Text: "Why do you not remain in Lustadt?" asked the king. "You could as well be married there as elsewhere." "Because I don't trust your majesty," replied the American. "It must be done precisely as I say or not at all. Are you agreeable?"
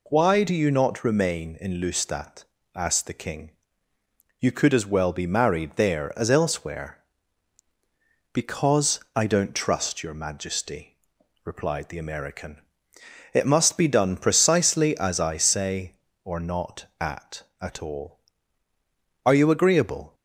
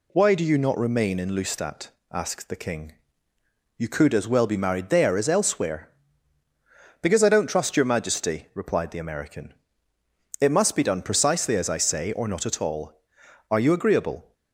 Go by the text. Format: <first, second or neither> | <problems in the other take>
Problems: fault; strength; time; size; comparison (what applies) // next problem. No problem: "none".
second | pauses between "Because" and "I"; slight; at 9.0 s; 0.16 s long // says "at" twice; at 17.6 s